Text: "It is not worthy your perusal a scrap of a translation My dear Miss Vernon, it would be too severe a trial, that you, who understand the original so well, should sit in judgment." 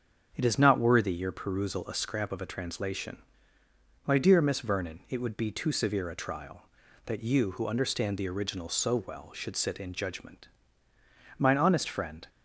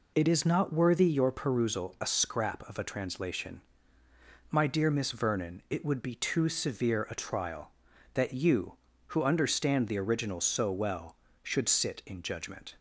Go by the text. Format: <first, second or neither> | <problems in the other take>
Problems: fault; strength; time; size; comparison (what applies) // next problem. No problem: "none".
second | starts louder than the rest; strong; until 1.3 s; 7 dB // pauses between "translation" and "My"; noticeable; at 3.2 s; 0.86 s long; noticeable in the second // goes on to say "Mine honest friend"; noticeable; from 11.3 s on; 0.92 s long